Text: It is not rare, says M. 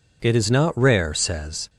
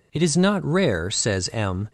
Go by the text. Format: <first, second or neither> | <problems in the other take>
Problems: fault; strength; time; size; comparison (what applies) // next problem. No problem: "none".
second | stops before "M"; at 1.6 s